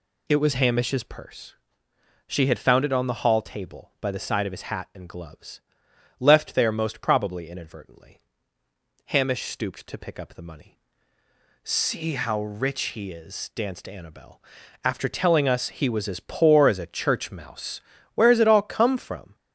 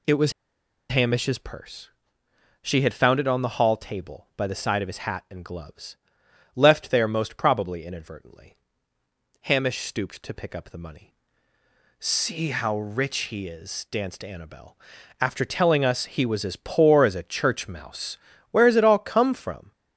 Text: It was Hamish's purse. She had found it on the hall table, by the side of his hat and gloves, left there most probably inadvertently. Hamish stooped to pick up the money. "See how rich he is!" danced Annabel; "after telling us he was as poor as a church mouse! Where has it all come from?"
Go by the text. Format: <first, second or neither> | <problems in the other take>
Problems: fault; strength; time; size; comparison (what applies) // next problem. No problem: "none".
first | pauses between "was" and "Hamish's"; noticeable; at 0.3 s; 0.57 s long